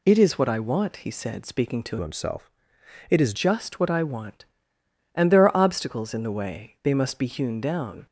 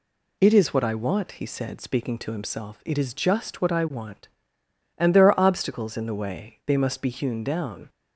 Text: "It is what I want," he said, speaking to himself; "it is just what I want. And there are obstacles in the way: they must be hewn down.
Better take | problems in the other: second | changes voice from "himself" to "is"; from 2.0 to 3.3 s; 1.3 s long

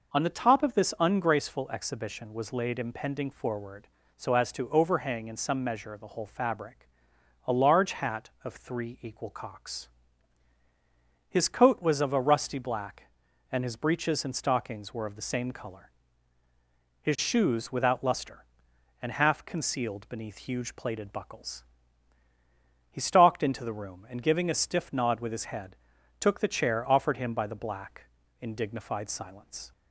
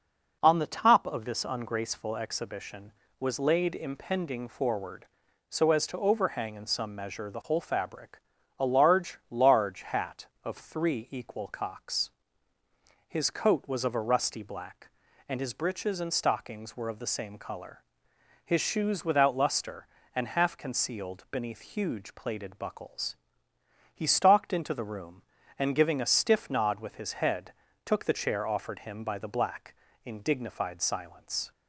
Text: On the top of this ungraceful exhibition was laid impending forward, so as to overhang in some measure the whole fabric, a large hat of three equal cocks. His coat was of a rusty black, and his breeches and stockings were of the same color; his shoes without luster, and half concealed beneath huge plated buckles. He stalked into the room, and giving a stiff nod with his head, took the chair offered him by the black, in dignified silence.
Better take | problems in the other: first | says "large" twice; at 9.2 s

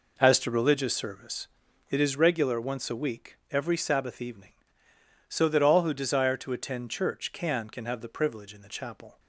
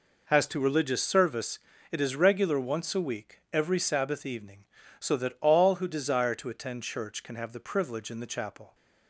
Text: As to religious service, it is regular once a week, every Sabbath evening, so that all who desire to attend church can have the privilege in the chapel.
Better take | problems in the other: second | says "can" twice; at 7.6 s

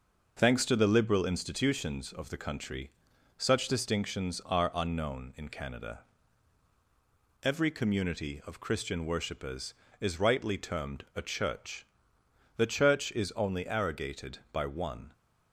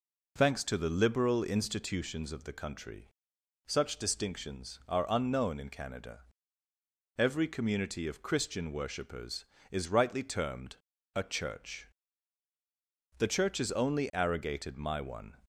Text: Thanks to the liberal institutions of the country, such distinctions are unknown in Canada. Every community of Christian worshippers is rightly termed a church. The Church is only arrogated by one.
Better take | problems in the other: first | pauses between "termed" and "a"; at 10.7 s; 0.38 s long // says "my" for "by"; at 14.7 s

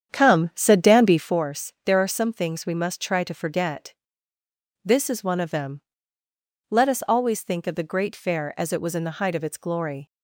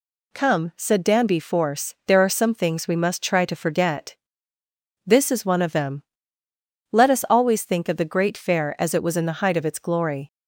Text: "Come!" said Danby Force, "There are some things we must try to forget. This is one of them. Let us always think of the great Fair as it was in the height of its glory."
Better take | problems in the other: second | starts louder than the rest; strong; until 1.4 s; 8.5 dB

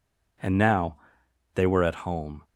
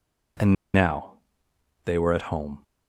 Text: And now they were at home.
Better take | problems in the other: first | pauses between "And" and "now"; slight; at 0.5 s; 0.20 s long // pauses between "now" and "they"; noticeable; at 1.1 s; 0.72 s long; noticeable in the first

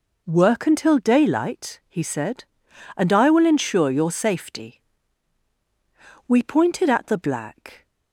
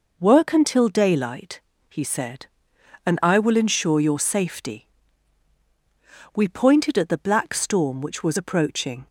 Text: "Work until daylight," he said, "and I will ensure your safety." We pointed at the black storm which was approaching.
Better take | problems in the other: second | stops before "storm which was approaching"; at 7.8 s

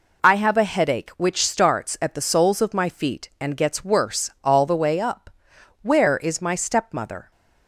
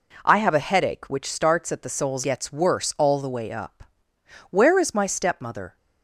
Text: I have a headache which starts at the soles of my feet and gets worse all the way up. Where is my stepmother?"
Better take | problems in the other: first | skips "of my feet and"; at 2.2 s

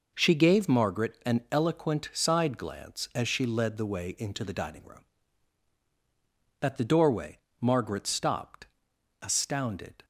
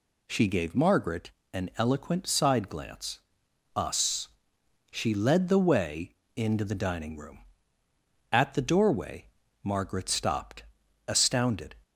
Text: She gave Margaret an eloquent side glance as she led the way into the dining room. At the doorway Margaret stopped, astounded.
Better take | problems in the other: first | pauses between "Margaret" and "an"; slight; at 1.3 s; 0.22 s long // says "us" for "as"; at 3.7 s // pauses between "way" and "into"; slight; at 6.1 s; 0.26 s long // pauses between "doorway" and "Margaret"; slight; at 9.2 s; 0.36 s long; slight in the first

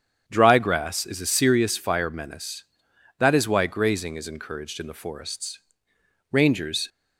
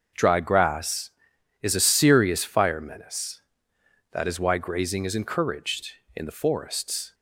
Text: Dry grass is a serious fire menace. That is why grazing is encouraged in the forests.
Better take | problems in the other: second | starts louder than the rest; strong; until 1.2 s; 8 dB; also in the second // goes on to say "Rangers"; from 6.3 s on; 0.56 s long

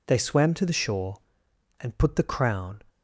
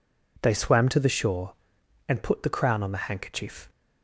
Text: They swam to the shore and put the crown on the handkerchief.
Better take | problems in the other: second | stops before "on the handkerchief"; at 2.8 s

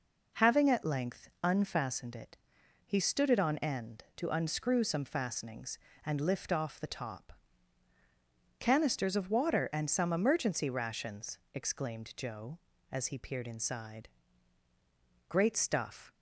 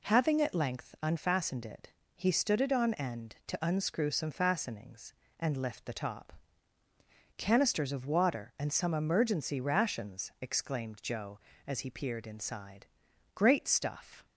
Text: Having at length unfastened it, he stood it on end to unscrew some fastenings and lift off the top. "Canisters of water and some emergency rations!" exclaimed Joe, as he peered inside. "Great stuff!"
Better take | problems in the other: first | skips "off"; at 5.8 s

